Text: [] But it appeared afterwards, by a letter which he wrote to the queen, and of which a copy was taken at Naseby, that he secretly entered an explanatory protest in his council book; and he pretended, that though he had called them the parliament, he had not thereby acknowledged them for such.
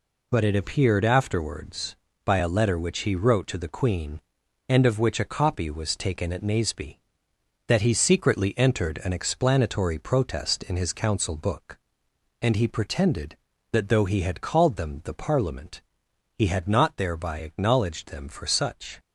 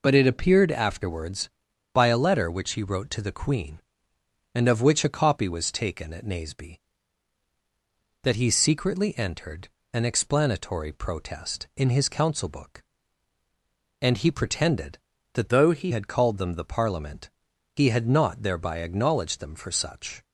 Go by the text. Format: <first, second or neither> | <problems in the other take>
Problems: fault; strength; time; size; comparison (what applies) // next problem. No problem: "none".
first | pauses between "entered" and "an"; slight; at 9.6 s; 0.24 s long // changes voice from "though" to "he"; from 15.4 to 15.9 s; 0.5 s long